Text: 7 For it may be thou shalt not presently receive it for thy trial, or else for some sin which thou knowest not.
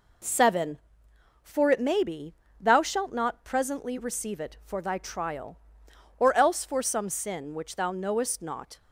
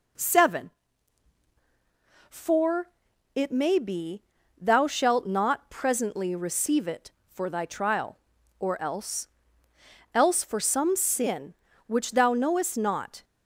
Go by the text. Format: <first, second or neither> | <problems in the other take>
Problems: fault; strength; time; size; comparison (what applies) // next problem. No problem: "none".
first | pauses between "For" and "it"; noticeable; at 2.8 s; 0.48 s long // pauses between "be" and "thou"; slight; at 4.2 s; 0.36 s long; slight in the first // says "else" twice; at 10.1 s